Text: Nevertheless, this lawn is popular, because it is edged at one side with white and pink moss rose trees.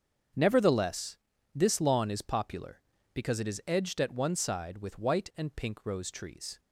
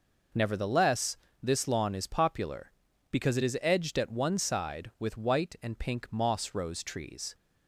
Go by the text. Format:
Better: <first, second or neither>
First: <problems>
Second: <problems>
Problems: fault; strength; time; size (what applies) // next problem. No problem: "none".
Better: second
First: starts louder than the rest; strong; until 1.7 s; 7.5 dB // skips "moss"; at 5.8 s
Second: none